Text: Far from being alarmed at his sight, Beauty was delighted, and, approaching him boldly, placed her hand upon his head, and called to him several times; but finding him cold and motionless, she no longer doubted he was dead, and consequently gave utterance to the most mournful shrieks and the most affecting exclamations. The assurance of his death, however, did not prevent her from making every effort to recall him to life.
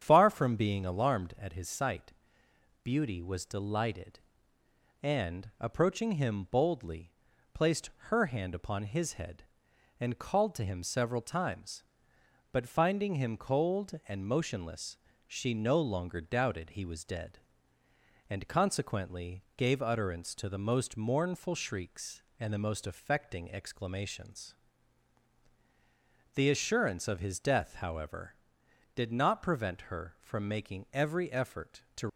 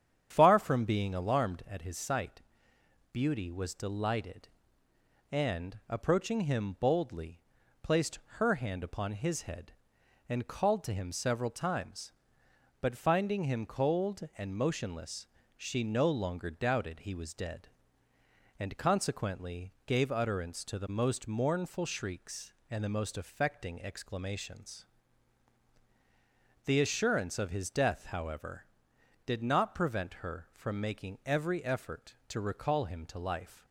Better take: second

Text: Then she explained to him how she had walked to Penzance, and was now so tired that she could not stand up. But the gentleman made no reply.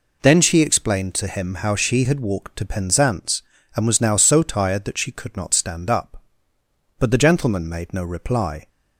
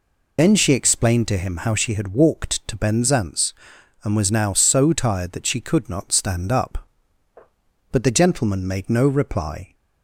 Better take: first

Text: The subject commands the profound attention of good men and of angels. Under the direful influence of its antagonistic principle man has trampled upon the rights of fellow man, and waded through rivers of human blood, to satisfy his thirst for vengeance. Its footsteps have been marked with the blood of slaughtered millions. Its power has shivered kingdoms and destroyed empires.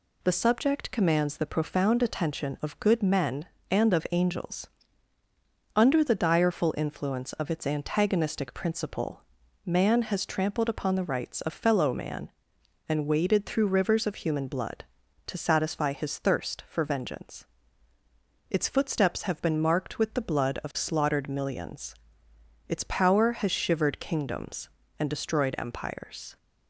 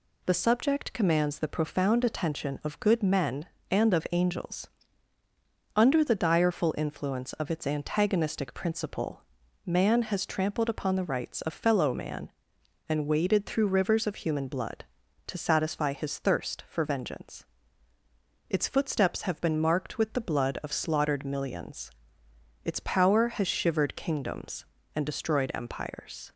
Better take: neither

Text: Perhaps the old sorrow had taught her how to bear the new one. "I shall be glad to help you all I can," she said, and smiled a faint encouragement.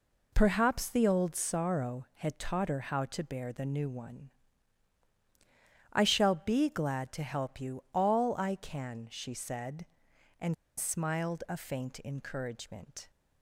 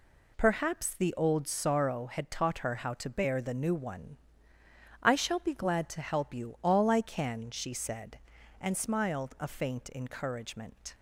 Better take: second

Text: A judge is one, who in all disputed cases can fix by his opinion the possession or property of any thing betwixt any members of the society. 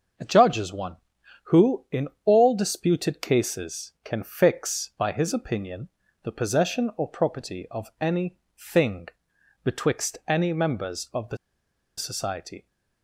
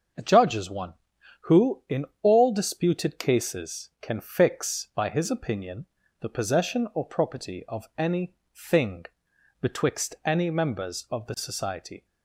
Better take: second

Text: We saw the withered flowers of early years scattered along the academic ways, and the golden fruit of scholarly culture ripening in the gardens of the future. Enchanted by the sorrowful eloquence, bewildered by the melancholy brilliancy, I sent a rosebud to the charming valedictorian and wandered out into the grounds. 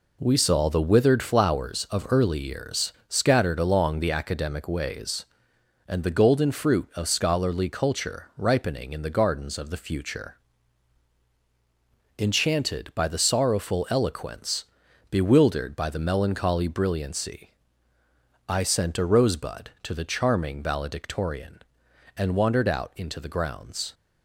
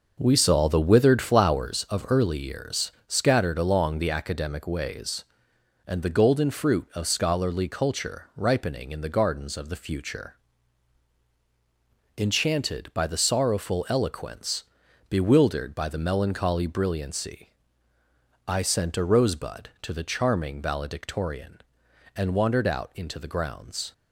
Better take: first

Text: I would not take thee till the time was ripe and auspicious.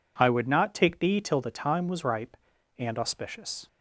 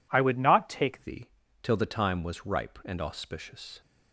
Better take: first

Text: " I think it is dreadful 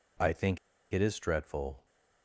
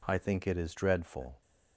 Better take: second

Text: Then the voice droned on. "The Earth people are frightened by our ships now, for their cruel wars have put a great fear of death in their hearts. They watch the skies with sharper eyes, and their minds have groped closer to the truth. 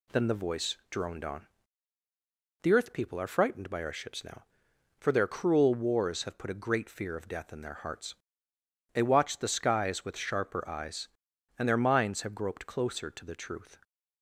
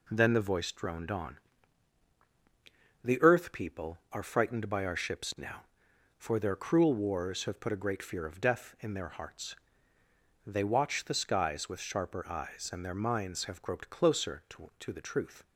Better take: first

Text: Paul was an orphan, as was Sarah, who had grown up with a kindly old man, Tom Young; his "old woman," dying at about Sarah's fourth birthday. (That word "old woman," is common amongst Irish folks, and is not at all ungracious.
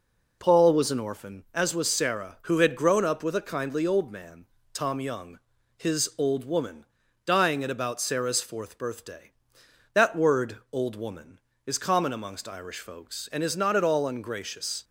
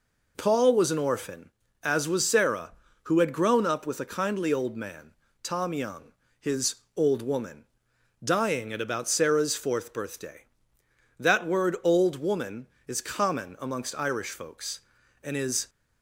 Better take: first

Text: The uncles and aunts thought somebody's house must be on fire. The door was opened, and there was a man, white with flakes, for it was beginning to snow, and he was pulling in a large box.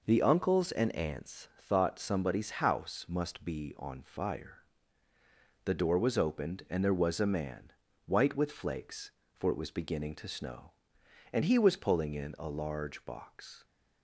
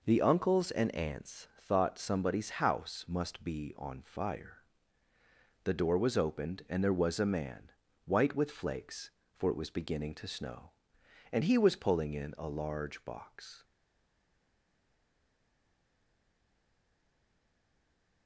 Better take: first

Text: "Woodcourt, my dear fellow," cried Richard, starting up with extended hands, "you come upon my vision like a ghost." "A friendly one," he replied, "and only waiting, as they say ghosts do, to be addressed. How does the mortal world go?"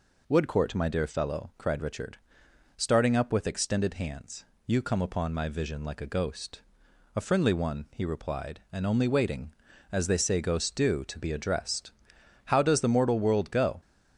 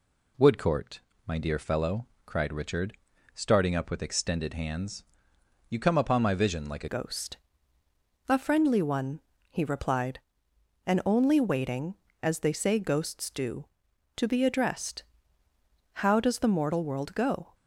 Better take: first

